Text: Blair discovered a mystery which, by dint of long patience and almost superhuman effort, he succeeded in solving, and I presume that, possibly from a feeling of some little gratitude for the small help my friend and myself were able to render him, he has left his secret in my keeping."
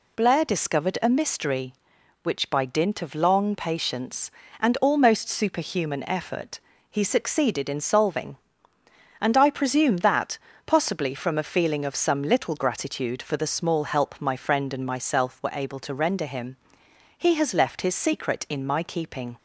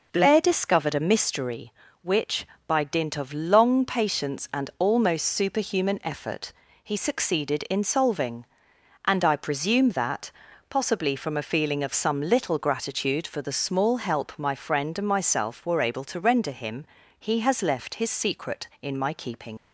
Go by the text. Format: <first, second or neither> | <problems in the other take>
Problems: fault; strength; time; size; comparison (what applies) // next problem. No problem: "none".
first | leaves "keeping" unfinished; at 19.5 s; 65 ms